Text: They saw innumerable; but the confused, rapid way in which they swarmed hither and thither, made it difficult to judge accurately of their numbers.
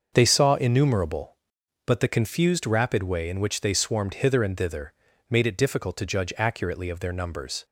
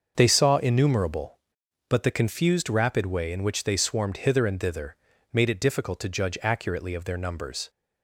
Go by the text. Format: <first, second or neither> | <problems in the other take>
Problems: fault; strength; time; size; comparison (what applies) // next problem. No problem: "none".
neither | starts louder than the rest; the same in both